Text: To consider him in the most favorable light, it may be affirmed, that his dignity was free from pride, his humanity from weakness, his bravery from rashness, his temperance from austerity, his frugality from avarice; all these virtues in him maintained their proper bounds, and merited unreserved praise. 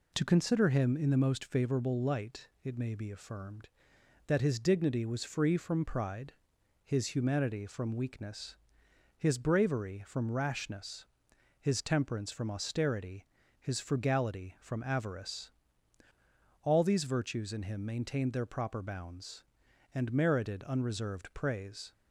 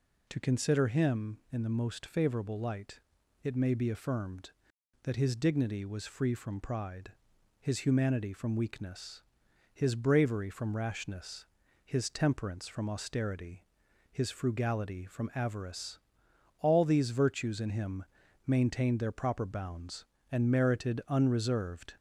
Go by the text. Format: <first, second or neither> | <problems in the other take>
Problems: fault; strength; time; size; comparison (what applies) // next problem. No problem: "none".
first | pauses between "him" and "maintained"; at 18.0 s; 0.42 s long // stops before "praise"; at 21.9 s